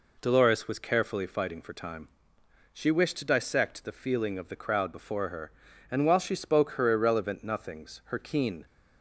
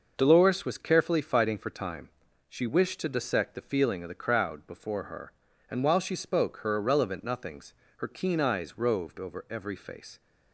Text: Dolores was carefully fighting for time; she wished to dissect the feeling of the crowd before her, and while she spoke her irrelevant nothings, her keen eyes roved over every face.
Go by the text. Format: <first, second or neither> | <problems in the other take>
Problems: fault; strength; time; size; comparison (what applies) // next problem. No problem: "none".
second | stops before "eyes roved over every face"; at 8.6 s